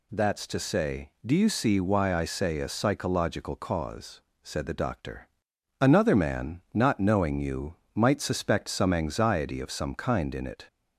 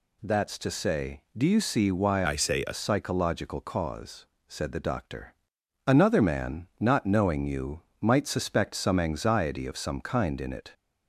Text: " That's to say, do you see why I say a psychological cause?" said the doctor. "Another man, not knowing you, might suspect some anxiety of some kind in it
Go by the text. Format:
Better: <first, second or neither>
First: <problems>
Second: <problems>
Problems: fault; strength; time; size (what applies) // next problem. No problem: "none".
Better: first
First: none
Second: changes voice from "I" to "a"; from 2.2 to 2.7 s; 0.5 s long